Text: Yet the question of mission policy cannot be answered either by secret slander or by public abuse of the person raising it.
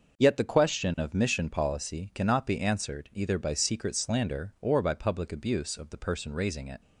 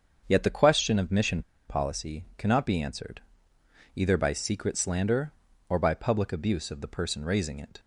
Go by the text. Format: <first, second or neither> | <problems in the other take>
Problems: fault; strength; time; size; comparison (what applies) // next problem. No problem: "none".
first | starts louder than the rest; until 1.2 s; 7 dB; noticeable in the first // pauses between "mission" and "policy"; slight; at 1.4 s; 0.25 s long // pauses between "answered" and "either"; noticeable; at 3.2 s; 0.74 s long